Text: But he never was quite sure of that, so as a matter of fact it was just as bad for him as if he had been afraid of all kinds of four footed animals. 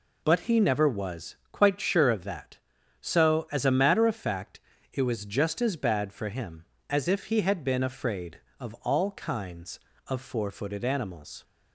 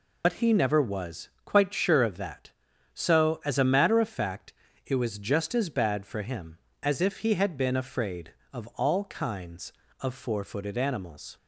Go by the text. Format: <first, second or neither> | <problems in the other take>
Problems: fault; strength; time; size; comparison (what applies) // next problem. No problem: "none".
first | loses the start of "But"; at 0.2 s; 85 ms // pauses between "was" and "quite"; slight; at 1.2 s; 0.16 s long; slight in the first // pauses between "fact" and "it"; slight; at 4.5 s; 0.34 s long; slight in the first